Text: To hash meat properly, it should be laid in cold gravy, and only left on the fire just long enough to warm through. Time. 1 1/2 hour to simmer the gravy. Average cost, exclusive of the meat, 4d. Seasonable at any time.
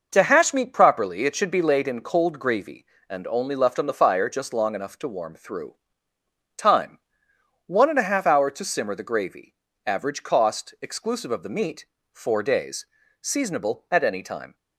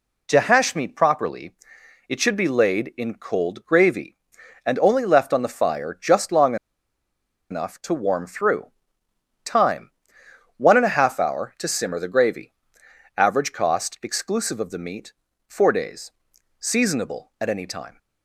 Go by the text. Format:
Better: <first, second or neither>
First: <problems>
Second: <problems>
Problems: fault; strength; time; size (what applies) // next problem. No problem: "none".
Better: first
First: none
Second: pauses between "long" and "enough"; noticeable; at 6.5 s; 0.95 s long